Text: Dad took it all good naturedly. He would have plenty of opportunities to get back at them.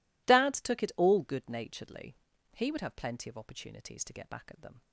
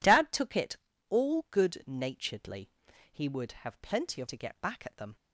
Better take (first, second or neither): first